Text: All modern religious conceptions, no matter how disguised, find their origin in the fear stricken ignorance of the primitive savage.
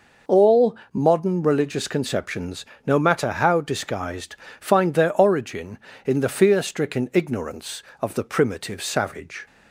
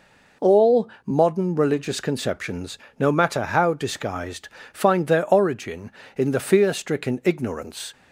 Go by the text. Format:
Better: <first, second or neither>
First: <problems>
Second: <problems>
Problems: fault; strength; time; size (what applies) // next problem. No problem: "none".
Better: first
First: pauses between "All" and "modern"; slight; at 0.7 s; 0.18 s long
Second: pauses between "All" and "modern"; slight; at 0.8 s; 0.18 s long // stops before "of the primitive savage"; at 7.9 s